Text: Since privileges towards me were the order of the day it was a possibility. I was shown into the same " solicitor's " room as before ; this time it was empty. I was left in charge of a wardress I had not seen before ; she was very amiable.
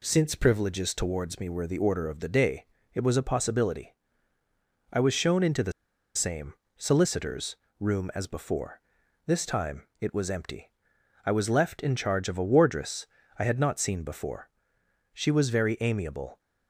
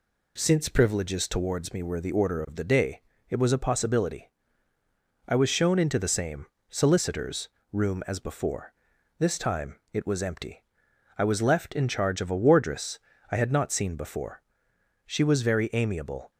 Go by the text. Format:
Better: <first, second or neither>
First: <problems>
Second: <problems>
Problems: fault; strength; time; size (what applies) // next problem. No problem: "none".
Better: second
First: pauses between "day" and "it"; slight; at 2.6 s; 0.28 s long // pauses between "the" and "same"; at 5.7 s; 0.44 s long // pauses between "wardress" and "I"; slight; at 13.0 s; 0.28 s long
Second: pauses between "day" and "it"; slight; at 3.0 s; 0.28 s long // pauses between "wardress" and "I"; slight; at 13.0 s; 0.28 s long